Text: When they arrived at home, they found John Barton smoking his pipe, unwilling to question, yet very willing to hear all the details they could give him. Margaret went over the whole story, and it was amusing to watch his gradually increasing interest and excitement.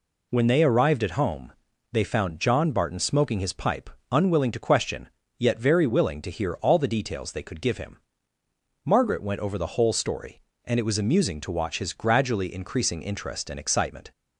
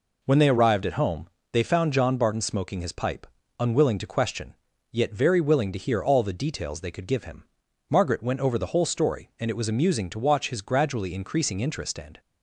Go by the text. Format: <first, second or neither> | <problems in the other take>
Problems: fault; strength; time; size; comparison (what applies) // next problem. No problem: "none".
first | stops before "excitement"; at 12.1 s